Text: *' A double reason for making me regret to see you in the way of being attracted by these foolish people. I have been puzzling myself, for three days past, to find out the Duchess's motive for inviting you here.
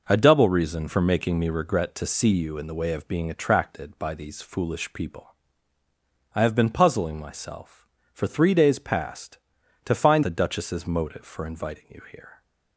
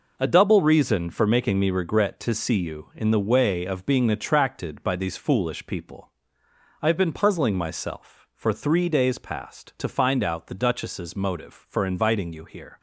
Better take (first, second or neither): second